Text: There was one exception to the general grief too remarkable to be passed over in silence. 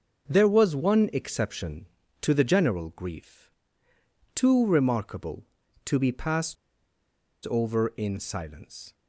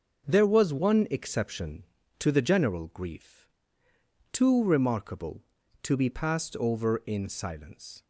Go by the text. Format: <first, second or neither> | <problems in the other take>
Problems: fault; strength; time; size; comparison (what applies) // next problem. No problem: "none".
second | starts louder than the rest; until 1.3 s; 6.5 dB; also in the second // pauses between "grief" and "too"; noticeable; at 3.4 s; 0.86 s long; noticeable in the second // pauses between "passed" and "over"; noticeable; at 6.5 s; 0.96 s long